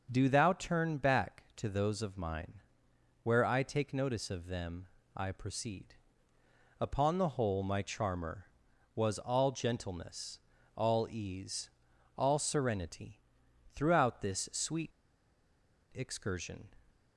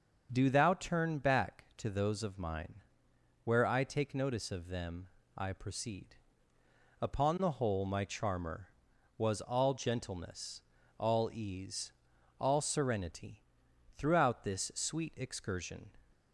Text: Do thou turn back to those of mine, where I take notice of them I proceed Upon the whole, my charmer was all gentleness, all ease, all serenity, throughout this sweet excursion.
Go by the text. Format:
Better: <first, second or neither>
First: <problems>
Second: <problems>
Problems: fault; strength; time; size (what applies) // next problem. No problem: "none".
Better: second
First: starts louder than the rest; noticeable; until 1.1 s; 6 dB // pauses between "them" and "I"; slight; at 4.8 s; 0.28 s long // pauses between "proceed" and "Upon"; noticeable; at 5.9 s; 0.88 s long // pauses between "sweet" and "excursion"; at 14.8 s; 1.0 s long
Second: starts louder than the rest; noticeable; until 1.3 s; 6 dB // pauses between "them" and "I"; slight; at 5.0 s; 0.28 s long // pauses between "proceed" and "Upon"; noticeable; at 6.1 s; 0.88 s long